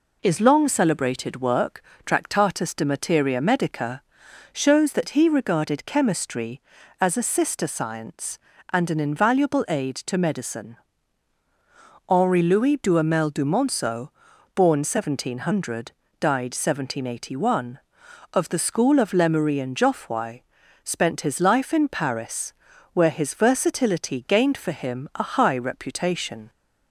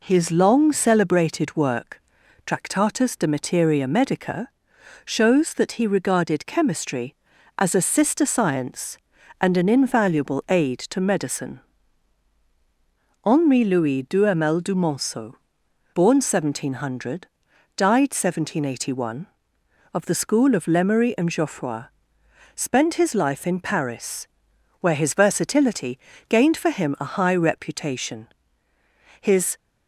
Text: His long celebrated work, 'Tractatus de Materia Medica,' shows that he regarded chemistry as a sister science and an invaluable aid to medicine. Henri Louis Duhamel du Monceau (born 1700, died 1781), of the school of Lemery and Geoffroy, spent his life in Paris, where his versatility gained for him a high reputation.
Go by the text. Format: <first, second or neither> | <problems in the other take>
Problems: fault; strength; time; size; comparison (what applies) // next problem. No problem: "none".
first | pauses between "versatility" and "gained"; slight; at 25.9 s; 0.30 s long // goes on to say "His"; slight; from 29.2 s on; 0.36 s long